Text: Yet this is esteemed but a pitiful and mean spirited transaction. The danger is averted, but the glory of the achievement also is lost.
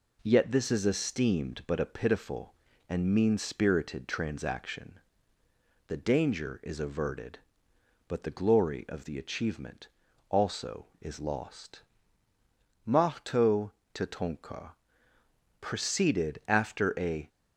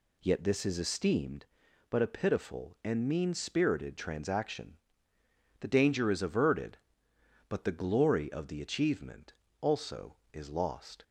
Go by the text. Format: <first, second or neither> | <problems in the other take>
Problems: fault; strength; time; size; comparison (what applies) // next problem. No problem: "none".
second | pauses between "achievement" and "also"; at 9.8 s; 0.40 s long; slight in the second // goes on to say "Mahto Tatonka proceeded after a"; strong; from 12.8 s on; 4.4 s long